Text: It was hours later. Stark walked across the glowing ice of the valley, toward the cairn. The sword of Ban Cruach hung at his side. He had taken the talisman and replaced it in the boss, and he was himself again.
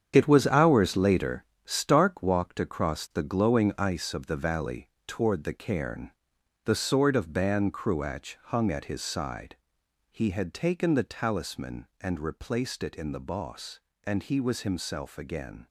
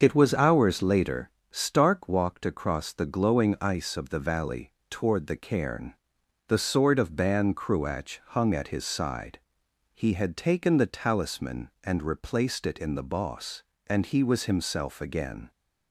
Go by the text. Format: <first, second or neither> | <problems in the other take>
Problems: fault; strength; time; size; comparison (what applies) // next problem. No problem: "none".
second | gets quieter; strong; throughout; 9.5 dB // starts louder than the rest; strong; until 1.1 s; 8 dB; also in the second